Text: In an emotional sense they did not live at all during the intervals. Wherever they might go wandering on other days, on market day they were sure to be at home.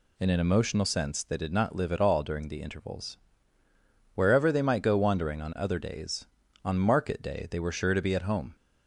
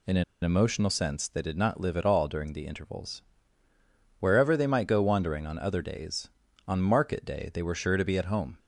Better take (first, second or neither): first